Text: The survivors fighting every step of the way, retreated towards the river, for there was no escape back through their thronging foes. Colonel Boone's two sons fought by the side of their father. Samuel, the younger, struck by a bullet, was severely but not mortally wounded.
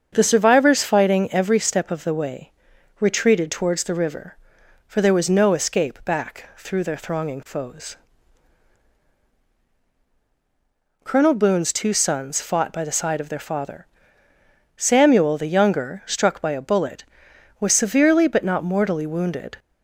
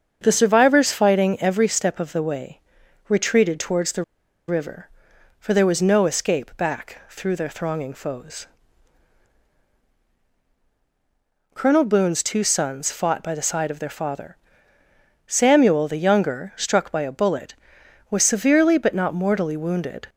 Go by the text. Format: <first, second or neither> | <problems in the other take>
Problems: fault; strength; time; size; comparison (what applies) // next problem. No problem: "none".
first | starts louder than the rest; until 1.2 s; 7 dB; also in the first // pauses between "the" and "river"; at 4.0 s; 0.43 s long